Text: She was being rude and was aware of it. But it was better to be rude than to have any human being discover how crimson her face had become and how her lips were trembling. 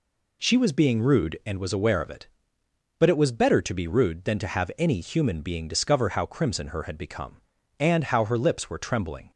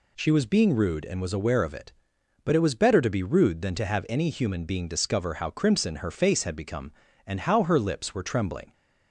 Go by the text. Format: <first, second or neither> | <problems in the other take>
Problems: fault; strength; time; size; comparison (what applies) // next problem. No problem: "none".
second | skips "face"; at 6.8 s